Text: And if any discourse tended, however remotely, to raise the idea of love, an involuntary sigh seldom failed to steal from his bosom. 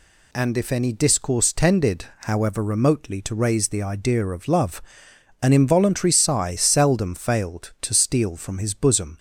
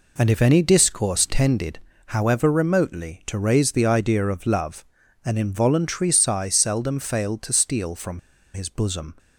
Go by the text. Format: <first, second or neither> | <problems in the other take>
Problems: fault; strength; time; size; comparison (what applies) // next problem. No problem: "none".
first | pauses between "from" and "his"; slight; at 8.1 s; 0.34 s long